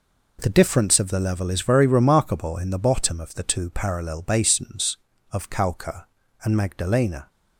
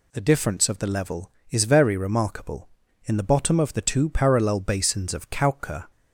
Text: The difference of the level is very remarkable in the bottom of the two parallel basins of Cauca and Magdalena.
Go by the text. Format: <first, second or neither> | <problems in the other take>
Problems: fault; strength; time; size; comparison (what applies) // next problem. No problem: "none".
first | stops before "and Magdalena"; at 5.9 s